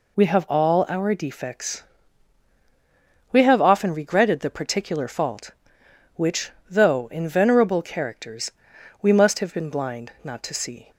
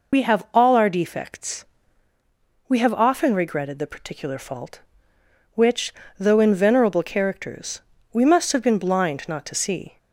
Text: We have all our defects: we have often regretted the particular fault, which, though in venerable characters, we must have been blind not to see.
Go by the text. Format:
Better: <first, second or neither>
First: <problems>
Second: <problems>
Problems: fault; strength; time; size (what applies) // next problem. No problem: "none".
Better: first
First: none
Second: loses the start of "We"; at 0.1 s; 55 ms